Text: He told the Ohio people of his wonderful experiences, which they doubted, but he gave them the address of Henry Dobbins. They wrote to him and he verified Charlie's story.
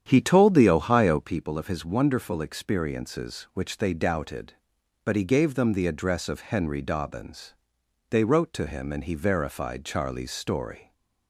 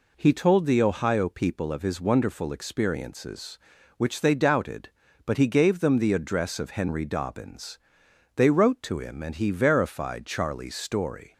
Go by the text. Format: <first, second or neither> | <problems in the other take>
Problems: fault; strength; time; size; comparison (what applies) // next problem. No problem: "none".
second | starts louder than the rest; strong; until 1.3 s; 9 dB